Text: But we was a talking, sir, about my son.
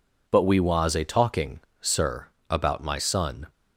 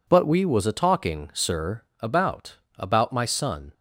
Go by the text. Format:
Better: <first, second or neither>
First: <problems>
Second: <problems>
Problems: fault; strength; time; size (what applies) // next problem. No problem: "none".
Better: first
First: none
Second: says "about" twice; at 2.7 s